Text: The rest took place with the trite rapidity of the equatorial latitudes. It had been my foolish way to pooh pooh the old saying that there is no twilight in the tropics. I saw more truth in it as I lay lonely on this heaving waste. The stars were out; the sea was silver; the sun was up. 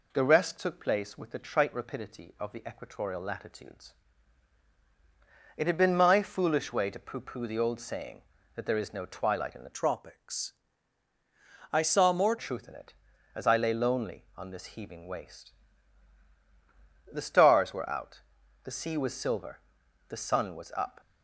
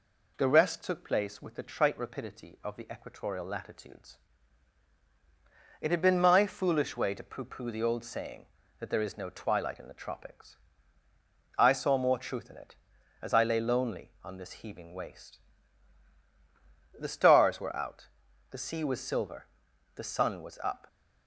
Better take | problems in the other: second | changes voice from "tropics" to "more"; from 9.7 to 12.3 s; 2.6 s long

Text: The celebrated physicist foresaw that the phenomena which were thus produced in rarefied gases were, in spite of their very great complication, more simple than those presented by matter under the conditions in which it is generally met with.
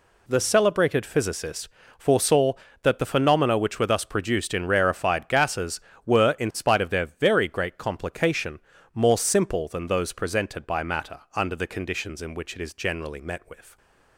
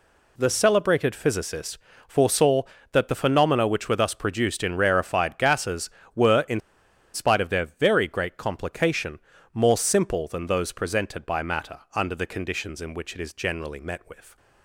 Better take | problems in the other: first | pauses between "physicist" and "foresaw"; slight; at 1.7 s; 0.28 s long; slight in the first // pauses between "in" and "spite"; noticeable; at 6.6 s; 0.53 s long // pauses between "matter" and "under"; slight; at 11.7 s; 0.16 s long; slight in the first

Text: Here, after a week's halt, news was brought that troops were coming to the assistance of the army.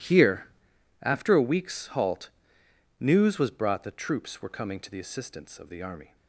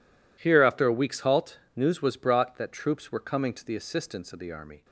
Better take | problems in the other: neither | none

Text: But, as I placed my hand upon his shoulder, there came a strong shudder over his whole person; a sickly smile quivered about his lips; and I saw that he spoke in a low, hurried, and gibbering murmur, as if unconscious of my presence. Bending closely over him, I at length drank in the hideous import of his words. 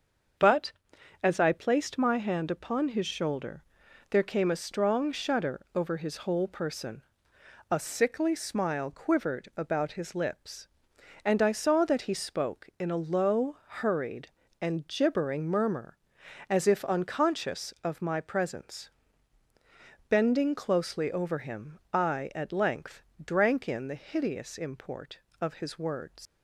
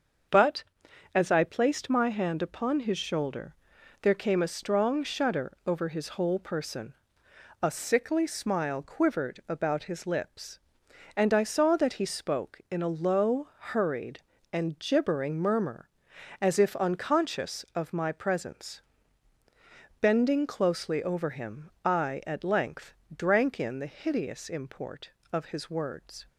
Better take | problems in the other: second | starts louder than the rest; until 1.8 s; 6.5 dB; also in the second // pauses between "length" and "drank"; slight; at 23.0 s; 0.22 s long; slight in the second // leaves "words" unfinished; at 26.2 s; 105 ms

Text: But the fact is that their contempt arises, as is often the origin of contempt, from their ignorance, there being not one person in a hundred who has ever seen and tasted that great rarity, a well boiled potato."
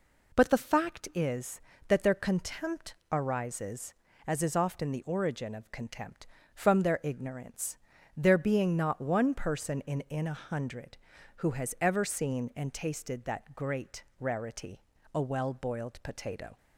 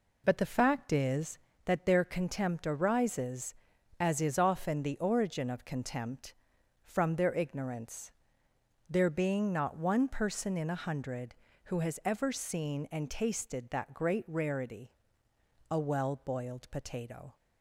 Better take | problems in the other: second | pauses between "contempt" and "arises"; slight; at 2.9 s; 0.16 s long // says "in" twice; at 10.0 s // pauses between "great" and "rarity"; slight; at 14.0 s; 0.16 s long

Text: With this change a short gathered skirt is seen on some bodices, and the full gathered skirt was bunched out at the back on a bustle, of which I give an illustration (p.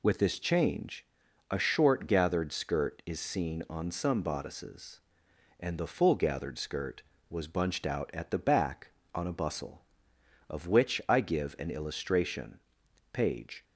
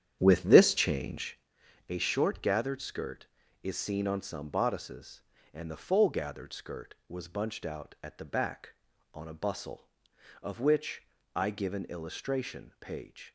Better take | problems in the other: first | starts louder than the rest; strong; until 1.5 s; 9.5 dB // pauses between "change" and "a"; noticeable; at 1.3 s; 0.50 s long; also in the first // pauses between "which" and "I"; slight; at 11.0 s; 0.30 s long

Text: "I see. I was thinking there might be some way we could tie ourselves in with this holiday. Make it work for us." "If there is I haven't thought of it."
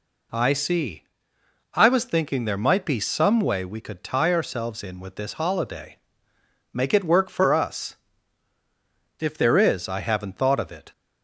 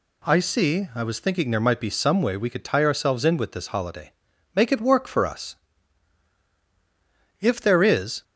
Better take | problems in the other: first | stops before "I haven't thought of it"; at 8.2 s

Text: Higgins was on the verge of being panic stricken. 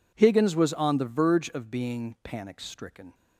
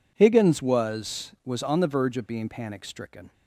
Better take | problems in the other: first | says "was" twice; at 1.4 s

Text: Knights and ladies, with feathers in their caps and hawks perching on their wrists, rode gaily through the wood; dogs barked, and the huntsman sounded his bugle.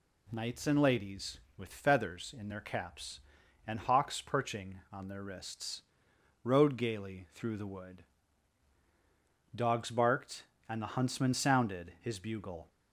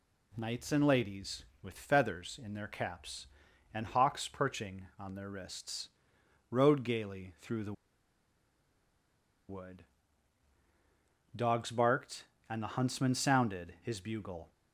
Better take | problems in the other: first | pauses between "the" and "wood"; strong; at 7.7 s; 1.7 s long

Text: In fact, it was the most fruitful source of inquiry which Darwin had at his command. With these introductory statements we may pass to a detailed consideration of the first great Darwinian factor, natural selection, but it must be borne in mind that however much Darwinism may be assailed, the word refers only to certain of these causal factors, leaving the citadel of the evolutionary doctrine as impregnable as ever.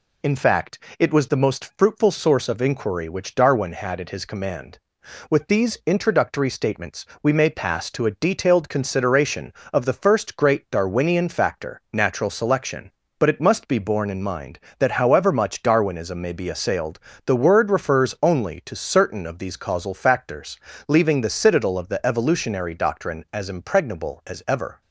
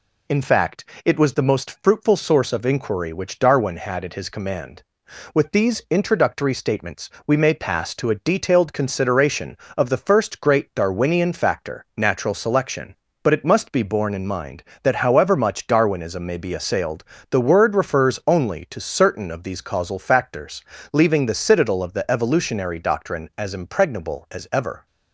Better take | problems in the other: neither | pauses between "statements" and "we"; slight; the same in both

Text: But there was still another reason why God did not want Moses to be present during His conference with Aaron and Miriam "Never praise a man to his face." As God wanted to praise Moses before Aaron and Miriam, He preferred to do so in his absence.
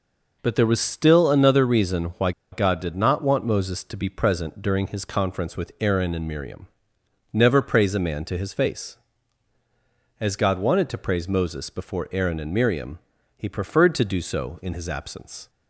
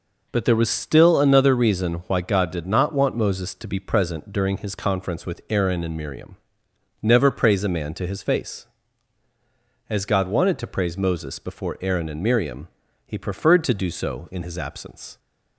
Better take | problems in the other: second | pauses between "why" and "God"; slight; at 2.3 s; 0.21 s long // pauses between "Miriam" and "Never"; noticeable; at 6.6 s; 0.64 s long; noticeable in the second

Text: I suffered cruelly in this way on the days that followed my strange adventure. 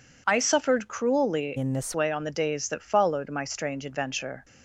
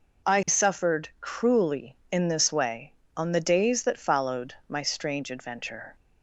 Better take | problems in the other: second | changes voice from "in" to "this"; from 1.5 to 1.9 s; 0.4 s long

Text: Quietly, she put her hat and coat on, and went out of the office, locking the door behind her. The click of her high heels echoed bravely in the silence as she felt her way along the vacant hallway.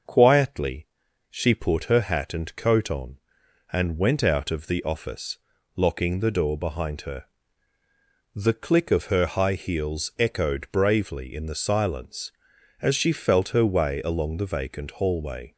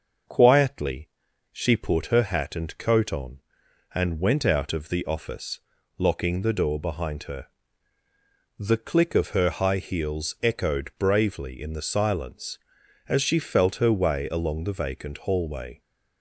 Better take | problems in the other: neither | starts louder than the rest; the same in both

